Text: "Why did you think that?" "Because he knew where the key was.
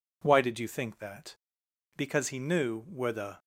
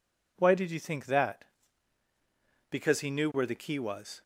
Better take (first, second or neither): second